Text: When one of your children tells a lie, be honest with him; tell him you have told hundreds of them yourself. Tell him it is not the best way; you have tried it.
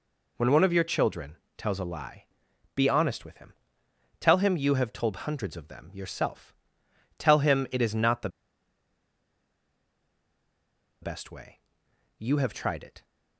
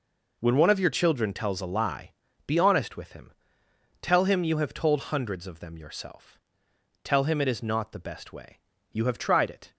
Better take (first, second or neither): second